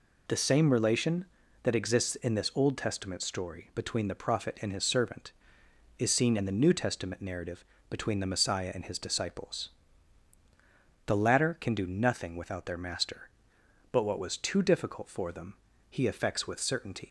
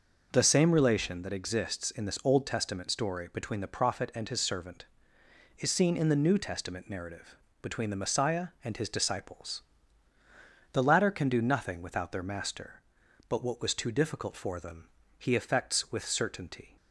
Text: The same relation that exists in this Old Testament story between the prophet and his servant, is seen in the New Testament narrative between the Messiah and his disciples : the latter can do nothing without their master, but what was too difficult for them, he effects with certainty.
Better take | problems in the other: second | pauses between "narrative" and "between"; slight; at 7.6 s; 0.24 s long; slight in the second // leaves "certainty" unfinished; at 17.0 s; 120 ms

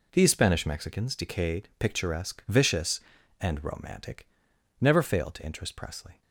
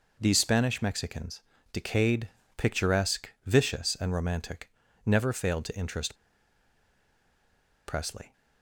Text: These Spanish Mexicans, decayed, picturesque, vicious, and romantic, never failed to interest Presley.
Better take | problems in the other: first | pauses between "interest" and "Presley"; strong; at 6.1 s; 1.7 s long

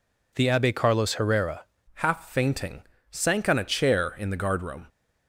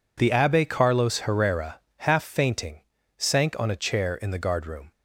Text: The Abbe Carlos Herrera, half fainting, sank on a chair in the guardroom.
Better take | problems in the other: second | changes voice at "half"; from 1.9 s on; 2.9 s long

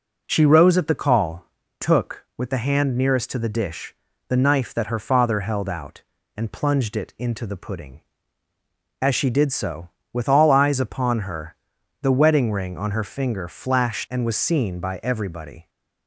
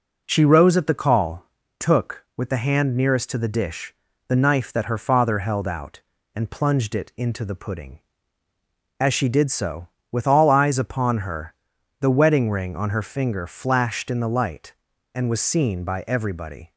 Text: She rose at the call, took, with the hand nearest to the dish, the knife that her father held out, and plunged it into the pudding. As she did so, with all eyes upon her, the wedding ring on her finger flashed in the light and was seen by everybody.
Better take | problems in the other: second | skips "in the light"; at 14.0 s

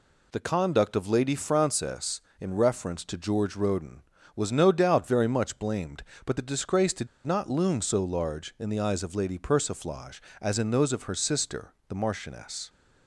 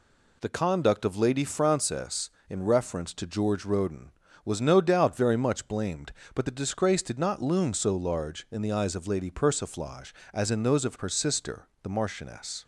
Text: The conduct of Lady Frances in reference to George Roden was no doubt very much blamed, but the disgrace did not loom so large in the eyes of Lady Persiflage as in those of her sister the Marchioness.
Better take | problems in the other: second | pauses between "did" and "not"; slight; at 7.0 s; 0.17 s long // pauses between "sister" and "the"; slight; at 11.7 s; 0.16 s long; slight in the second

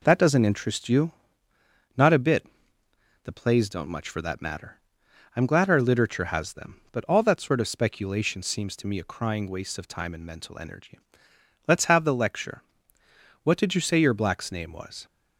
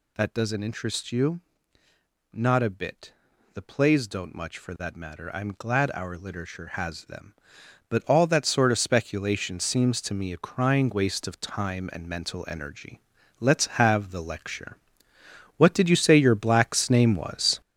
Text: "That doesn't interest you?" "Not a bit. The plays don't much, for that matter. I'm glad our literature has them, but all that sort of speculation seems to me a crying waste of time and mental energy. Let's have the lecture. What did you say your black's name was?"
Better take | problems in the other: first | gets louder; strong; throughout; 7.5 dB

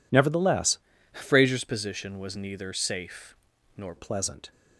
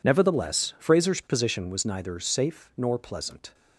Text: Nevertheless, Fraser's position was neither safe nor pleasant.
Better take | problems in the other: second | changes voice from "Fraser's" to "nor"; from 1.1 to 3.9 s; 2.8 s long // pauses between "safe" and "nor"; at 3.3 s; 0.42 s long

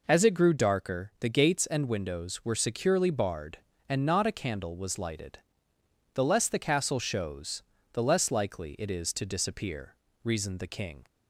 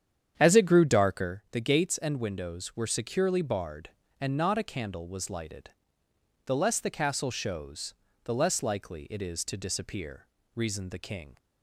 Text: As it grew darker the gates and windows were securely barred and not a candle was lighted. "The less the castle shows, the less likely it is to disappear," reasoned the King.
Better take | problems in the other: first | starts louder than the rest; strong; until 1.3 s; 8.5 dB

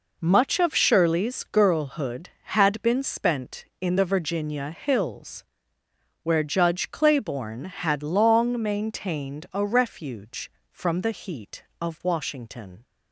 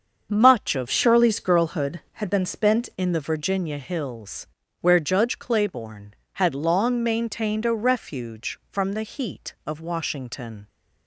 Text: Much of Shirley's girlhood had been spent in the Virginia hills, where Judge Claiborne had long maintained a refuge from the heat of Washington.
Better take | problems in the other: first | starts louder than the rest; until 1.3 s; 7 dB // changes voice from "Shirley's" to "spent"; from 0.9 to 2.9 s; 2.0 s long

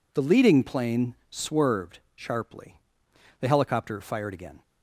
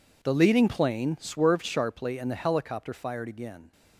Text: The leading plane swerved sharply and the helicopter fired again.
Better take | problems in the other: second | pauses between "plane" and "swerved"; slight; at 1.1 s; 0.16 s long // pauses between "swerved" and "sharply"; slight; at 1.9 s; 0.16 s long // skips "and"; at 3.0 s

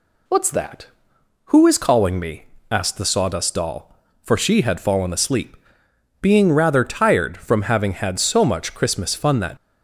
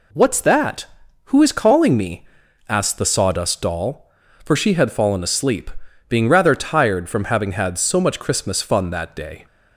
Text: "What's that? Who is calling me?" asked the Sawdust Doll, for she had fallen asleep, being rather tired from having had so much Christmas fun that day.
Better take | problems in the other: second | stops before "day"; at 9.5 s

